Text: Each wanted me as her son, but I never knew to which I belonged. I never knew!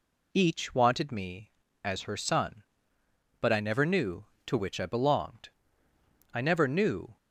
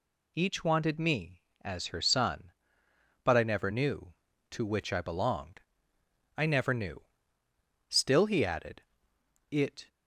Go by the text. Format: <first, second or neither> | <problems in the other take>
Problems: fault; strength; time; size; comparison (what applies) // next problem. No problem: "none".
first | goes on to say "Still he added it"; strong; from 7.9 s on; 1.9 s long